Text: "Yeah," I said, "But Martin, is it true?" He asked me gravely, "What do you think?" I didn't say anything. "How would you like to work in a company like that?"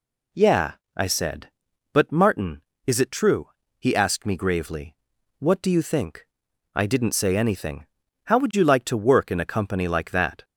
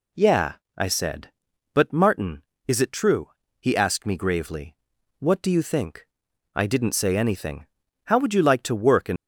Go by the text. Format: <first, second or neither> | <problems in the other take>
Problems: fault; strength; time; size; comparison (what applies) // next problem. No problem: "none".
first | stops before "a company like that"; at 9.1 s